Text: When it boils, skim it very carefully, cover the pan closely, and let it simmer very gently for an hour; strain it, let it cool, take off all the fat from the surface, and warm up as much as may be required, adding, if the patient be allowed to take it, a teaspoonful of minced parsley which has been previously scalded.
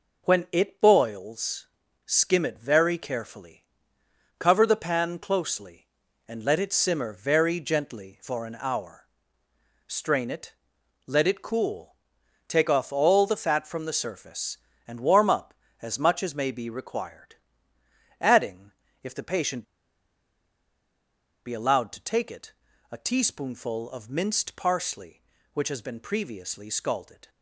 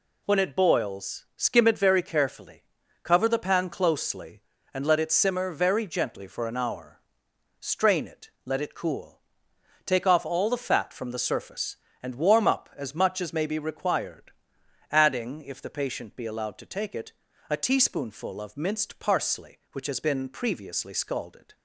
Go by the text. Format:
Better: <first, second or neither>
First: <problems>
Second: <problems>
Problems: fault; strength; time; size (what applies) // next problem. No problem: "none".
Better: second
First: pauses between "patient" and "be"; strong; at 19.6 s; 1.8 s long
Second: none